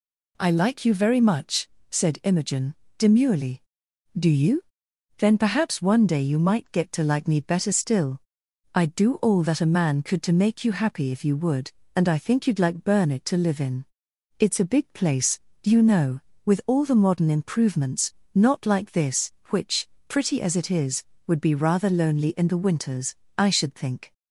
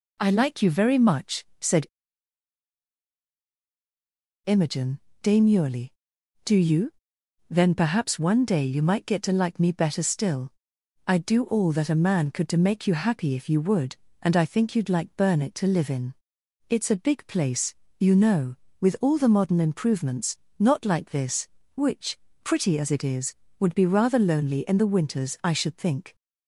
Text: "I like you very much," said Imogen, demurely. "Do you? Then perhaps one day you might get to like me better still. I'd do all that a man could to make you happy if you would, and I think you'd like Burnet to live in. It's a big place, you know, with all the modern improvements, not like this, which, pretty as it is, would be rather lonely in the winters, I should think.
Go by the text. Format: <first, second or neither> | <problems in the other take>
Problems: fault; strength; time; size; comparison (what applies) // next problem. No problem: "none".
first | pauses between "said" and "Imogen"; strong; at 1.8 s; 2.5 s long